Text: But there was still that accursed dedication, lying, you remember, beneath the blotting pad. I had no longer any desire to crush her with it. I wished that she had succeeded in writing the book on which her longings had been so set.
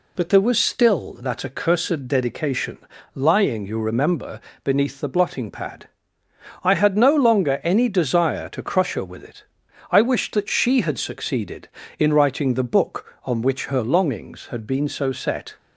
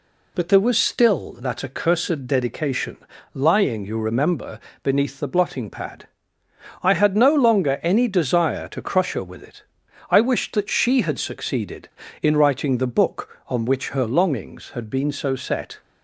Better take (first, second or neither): neither